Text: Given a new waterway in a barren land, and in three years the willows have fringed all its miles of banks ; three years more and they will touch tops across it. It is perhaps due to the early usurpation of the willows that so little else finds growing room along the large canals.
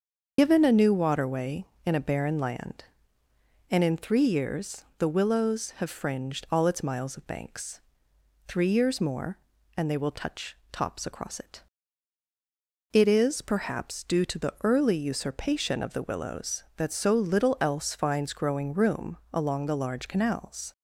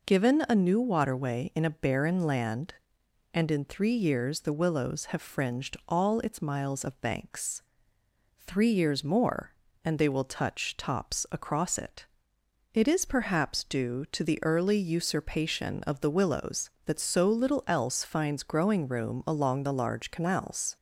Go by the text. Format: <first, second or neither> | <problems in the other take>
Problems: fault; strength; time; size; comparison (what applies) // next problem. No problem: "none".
second | loses the start of "Given"; at 0.3 s; 65 ms // starts louder than the rest; until 1.3 s; 6.5 dB // pauses between "touch" and "tops"; slight; at 10.5 s; 0.16 s long // pauses between "room" and "along"; slight; at 19.1 s; 0.16 s long